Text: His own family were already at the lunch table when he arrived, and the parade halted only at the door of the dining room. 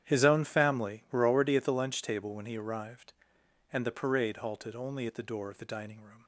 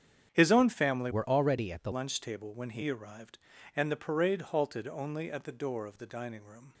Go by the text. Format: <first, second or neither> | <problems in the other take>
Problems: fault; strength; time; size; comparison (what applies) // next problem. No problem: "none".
first | starts louder than the rest; strong; until 1.3 s; 8 dB; strong in the first // changes voice from "were" to "the"; from 1.1 to 1.9 s; 0.8 s long